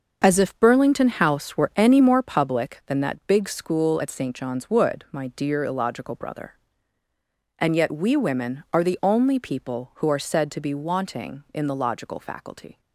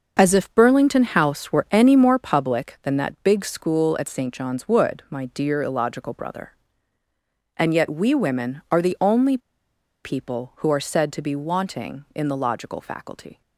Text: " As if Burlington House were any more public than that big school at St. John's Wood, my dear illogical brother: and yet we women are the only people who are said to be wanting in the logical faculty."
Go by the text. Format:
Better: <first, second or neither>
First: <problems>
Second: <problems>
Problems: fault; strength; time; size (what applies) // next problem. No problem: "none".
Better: first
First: starts louder than the rest; until 1.2 s; 6.5 dB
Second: starts louder than the rest; until 1.2 s; 6 dB // pauses between "only" and "people"; noticeable; at 9.3 s; 0.66 s long